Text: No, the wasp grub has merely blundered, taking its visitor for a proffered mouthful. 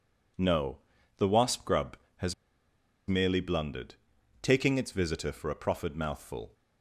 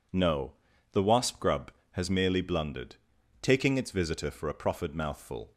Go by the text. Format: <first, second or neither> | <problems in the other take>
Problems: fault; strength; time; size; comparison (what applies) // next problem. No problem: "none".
second | pauses between "has" and "merely"; noticeable; at 2.3 s; 0.73 s long